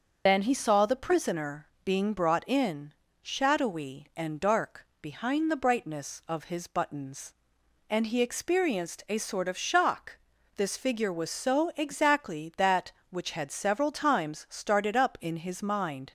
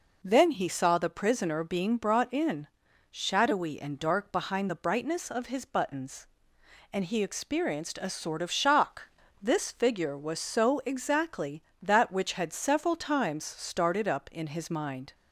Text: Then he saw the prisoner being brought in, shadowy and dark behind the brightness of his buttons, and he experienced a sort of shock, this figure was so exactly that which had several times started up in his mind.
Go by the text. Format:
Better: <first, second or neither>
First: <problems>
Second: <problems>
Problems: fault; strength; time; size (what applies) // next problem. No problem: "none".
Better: second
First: loses the start of "Then"; at 0.2 s; 85 ms // starts louder than the rest; until 1.2 s; 6.5 dB // pauses between "prisoner" and "being"; slight; at 1.6 s; 0.16 s long // pauses between "dark" and "behind"; slight; at 4.8 s; 0.16 s long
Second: none